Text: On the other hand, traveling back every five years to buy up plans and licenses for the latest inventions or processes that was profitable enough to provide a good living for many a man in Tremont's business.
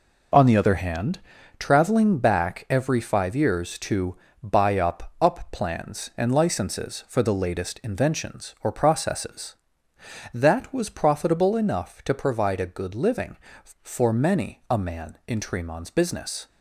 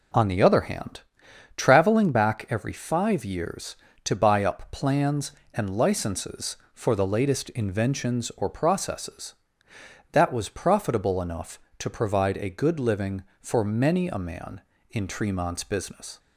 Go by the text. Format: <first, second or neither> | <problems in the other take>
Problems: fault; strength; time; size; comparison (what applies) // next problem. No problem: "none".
second | pauses between "to" and "buy"; slight; at 4.1 s; 0.26 s long // says "up" twice; at 5.2 s